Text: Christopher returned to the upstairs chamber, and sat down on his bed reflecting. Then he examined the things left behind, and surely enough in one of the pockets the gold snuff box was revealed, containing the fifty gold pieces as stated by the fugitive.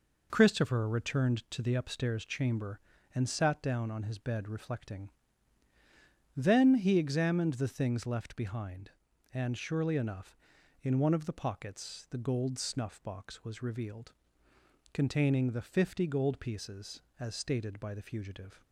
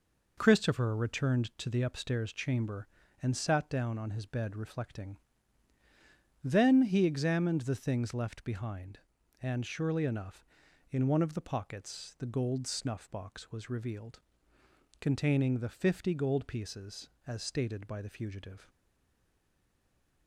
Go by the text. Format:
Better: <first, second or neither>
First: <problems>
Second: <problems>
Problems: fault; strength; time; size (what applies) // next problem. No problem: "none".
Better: first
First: none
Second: stays silent after the last word; noticeable; from 18.6 s on; 1.6 s long